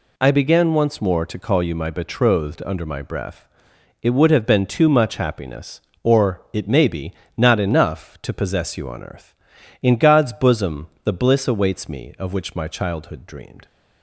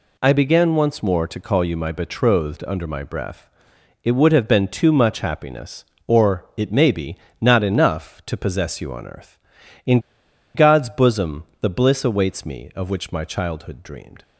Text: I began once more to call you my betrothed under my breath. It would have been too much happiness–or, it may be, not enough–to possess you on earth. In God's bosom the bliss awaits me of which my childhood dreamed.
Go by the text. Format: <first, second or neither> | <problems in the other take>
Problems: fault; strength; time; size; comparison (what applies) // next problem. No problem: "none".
first | pauses between "In" and "God's"; noticeable; at 9.9 s; 0.55 s long // pauses between "bosom" and "the"; slight; at 11.4 s; 0.18 s long; slight in the first